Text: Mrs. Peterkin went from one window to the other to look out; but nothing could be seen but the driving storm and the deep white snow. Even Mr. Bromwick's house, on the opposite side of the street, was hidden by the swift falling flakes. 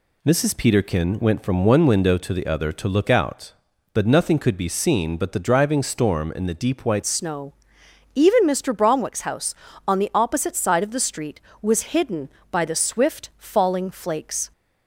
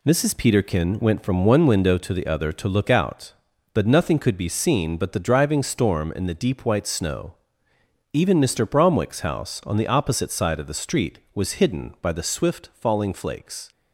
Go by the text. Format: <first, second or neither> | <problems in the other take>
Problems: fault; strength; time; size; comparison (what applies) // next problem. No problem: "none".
second | changes voice at "snow"; from 7.0 s on; 7.5 s long